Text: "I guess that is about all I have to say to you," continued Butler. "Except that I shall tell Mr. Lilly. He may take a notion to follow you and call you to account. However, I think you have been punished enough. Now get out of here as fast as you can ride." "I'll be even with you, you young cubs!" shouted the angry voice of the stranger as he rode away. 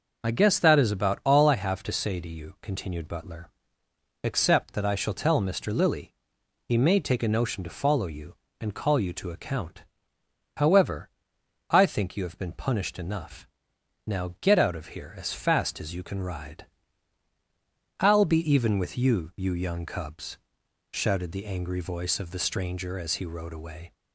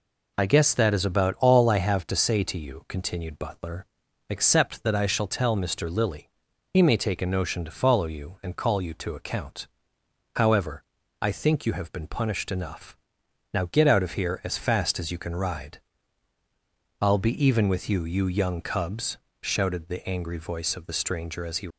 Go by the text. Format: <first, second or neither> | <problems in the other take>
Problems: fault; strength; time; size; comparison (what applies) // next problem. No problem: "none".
first | stops before "rode away"; at 21.6 s